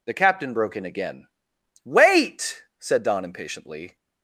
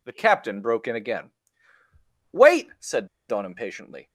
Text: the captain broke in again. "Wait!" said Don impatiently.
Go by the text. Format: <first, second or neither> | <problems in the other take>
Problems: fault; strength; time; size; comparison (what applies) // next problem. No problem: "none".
first | pauses between "said" and "Don"; slight; at 3.0 s; 0.21 s long